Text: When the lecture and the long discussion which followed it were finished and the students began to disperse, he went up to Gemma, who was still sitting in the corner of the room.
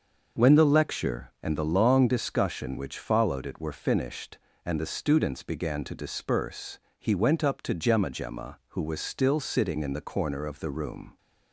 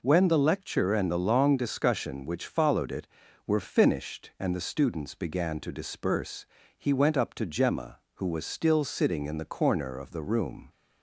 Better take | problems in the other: second | starts louder than the rest; noticeable; until 1.4 s; 6 dB // says "Gemma" twice; at 8.1 s

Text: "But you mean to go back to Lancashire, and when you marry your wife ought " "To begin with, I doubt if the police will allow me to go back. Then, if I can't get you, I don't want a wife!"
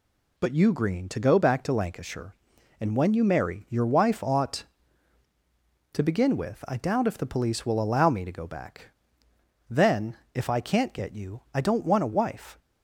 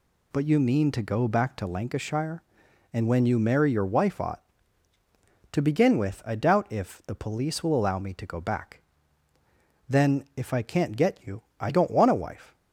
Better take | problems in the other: second | says "green" for "mean"; at 0.7 s

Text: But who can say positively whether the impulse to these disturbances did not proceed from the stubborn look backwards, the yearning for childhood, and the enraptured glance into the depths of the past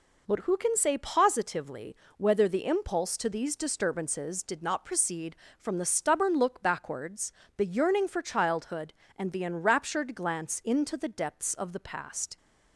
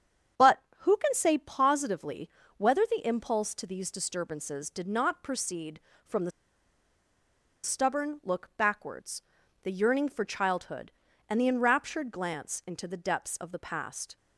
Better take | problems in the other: first | starts louder than the rest; strong; until 1.5 s; 8 dB // pauses between "positively" and "whether"; slight; at 2.2 s; 0.28 s long; slight in the first // pauses between "the" and "stubborn"; strong; at 6.3 s; 1.3 s long

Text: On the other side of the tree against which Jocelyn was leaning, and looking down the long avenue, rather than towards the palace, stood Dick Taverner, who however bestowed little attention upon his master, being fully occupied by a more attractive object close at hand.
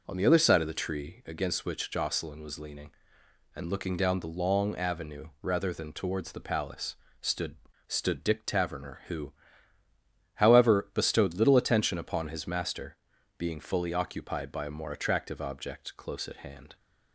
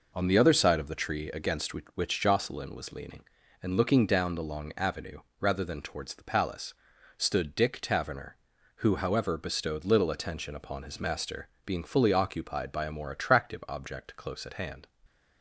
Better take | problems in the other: second | says "stood" twice; at 7.8 s // pauses between "who" and "however"; at 9.3 s; 1.0 s long

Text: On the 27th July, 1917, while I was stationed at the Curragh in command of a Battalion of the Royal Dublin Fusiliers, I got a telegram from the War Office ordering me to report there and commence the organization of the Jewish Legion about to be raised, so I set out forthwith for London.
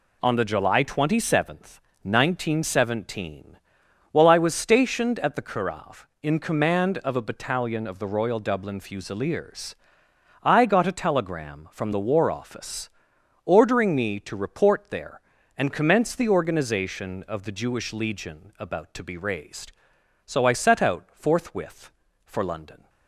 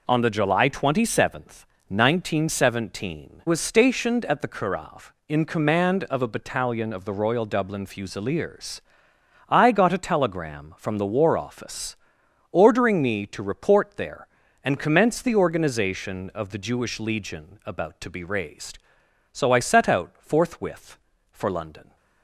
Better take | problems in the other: first | skips "while I"; at 3.4 s // pauses between "Office" and "ordering"; noticeable; at 11.9 s; 0.56 s long; noticeable in the first

